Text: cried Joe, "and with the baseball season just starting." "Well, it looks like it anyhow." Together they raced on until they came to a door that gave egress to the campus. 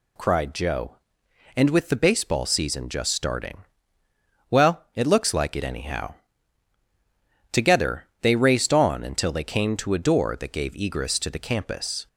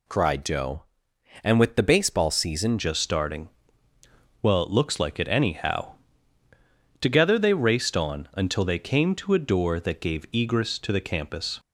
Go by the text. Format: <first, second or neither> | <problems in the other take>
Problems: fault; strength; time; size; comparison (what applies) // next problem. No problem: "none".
first | changes voice at "just"; from 2.7 s on; 8.8 s long